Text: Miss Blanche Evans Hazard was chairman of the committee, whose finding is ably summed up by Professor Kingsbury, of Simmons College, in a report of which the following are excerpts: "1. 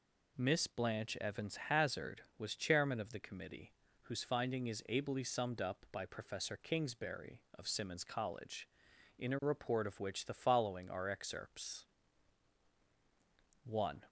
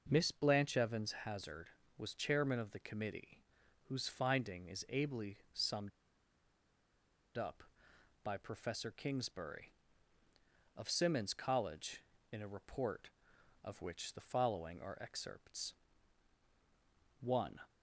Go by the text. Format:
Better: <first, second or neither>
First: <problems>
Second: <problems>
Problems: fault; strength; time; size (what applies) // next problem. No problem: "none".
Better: first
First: none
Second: pauses between "ably" and "summed"; slight; at 5.3 s; 0.16 s long // pauses between "summed" and "up"; strong; at 5.9 s; 1.4 s long